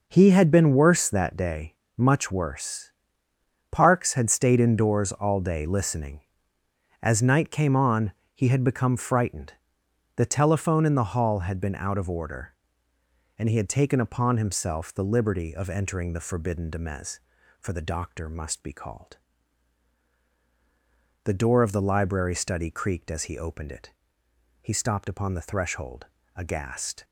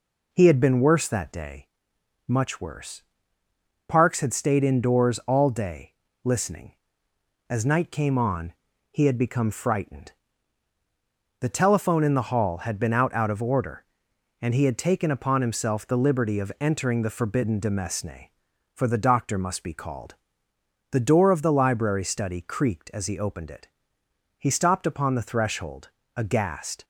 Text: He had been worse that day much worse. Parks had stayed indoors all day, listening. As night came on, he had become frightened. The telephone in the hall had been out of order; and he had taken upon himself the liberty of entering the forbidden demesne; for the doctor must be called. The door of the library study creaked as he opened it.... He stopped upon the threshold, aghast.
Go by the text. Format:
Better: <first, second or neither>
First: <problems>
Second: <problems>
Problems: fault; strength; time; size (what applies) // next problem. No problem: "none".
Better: first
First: pauses between "day" and "much"; slight; at 1.7 s; 0.26 s long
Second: pauses between "day" and "much"; noticeable; at 1.6 s; 0.60 s long // says "out" twice; at 13.1 s